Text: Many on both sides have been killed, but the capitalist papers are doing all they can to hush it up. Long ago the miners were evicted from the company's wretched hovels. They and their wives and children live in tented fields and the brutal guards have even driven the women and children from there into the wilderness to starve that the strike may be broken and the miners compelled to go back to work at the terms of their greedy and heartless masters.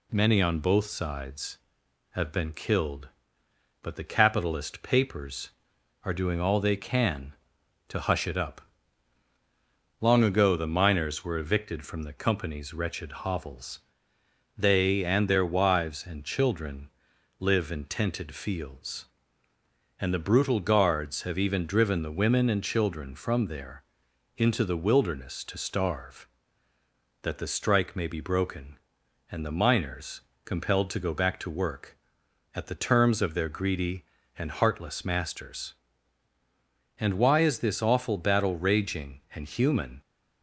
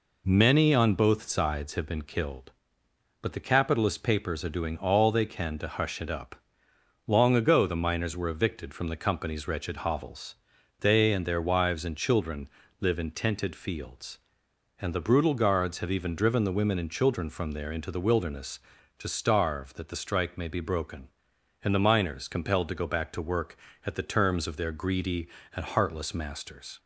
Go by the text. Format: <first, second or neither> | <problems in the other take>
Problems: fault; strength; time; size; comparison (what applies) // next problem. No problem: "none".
second | pauses between "children" and "live"; noticeable; at 16.8 s; 0.50 s long; slight in the second // pauses between "there" and "into"; noticeable; at 23.8 s; 0.52 s long // pauses between "miners" and "compelled"; slight; at 30.2 s; 0.24 s long // goes on to say "And why is this awful battle raging and human"; strong; from 36.9 s on; 3.0 s long